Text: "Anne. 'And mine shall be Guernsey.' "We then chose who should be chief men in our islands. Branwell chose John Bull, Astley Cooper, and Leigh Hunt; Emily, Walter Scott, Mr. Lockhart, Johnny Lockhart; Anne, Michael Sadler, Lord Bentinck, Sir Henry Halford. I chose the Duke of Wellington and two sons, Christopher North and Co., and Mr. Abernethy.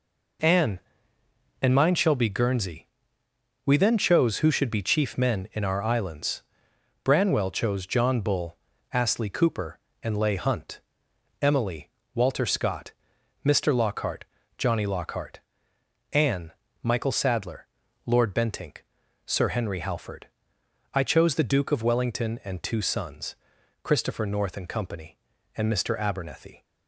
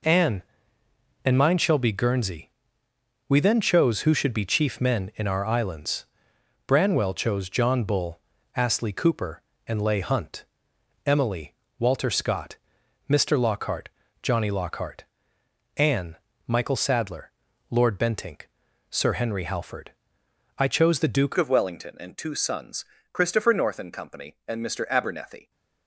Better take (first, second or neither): first